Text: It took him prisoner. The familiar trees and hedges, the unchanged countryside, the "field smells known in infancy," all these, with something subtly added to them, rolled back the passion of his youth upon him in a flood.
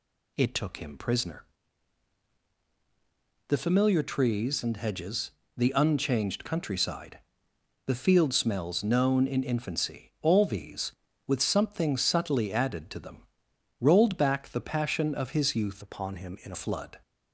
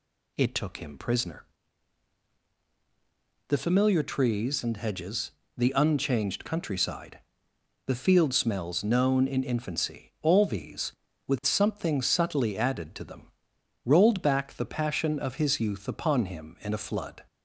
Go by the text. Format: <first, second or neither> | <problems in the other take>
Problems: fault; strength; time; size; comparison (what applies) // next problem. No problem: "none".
second | changes voice from "upon" to "a"; from 15.8 to 16.5 s; 0.7 s long